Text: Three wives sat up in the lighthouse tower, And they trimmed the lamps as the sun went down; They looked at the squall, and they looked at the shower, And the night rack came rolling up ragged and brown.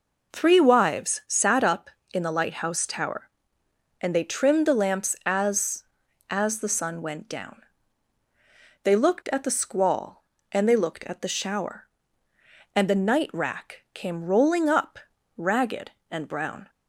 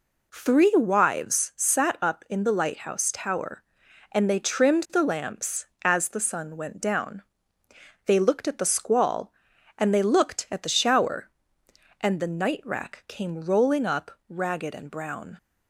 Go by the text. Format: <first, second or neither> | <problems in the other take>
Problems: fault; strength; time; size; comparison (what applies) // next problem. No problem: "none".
second | says "as" twice; at 6.3 s // pauses between "up" and "ragged"; at 14.9 s; 0.38 s long; slight in the second